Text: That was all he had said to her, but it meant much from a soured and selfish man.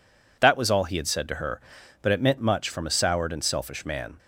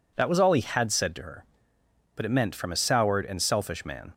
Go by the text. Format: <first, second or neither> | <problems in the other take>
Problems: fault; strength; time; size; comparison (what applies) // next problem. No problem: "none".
first | skips "much"; at 2.5 s